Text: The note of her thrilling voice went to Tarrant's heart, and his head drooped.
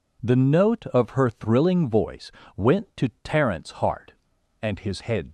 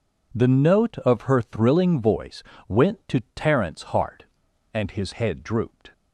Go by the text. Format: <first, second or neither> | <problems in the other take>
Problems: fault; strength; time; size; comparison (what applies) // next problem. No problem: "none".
second | pauses between "voice" and "went"; slight; at 2.3 s; 0.24 s long; slight in the second // stops before "drooped"; at 5.2 s